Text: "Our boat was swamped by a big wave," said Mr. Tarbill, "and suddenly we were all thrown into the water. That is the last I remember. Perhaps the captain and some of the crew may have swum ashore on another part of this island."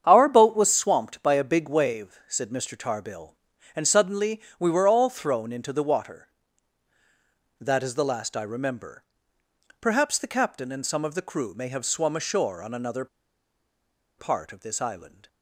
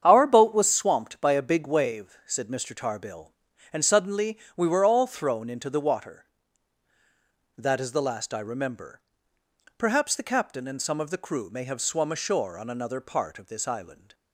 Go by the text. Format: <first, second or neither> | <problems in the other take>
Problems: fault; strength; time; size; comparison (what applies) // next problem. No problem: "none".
second | starts louder than the rest; strong; until 1.0 s; 8 dB; strong in the second // pauses between "suddenly" and "we"; slight; at 4.4 s; 0.16 s long; slight in the second // pauses between "another" and "part"; at 13.0 s; 1.1 s long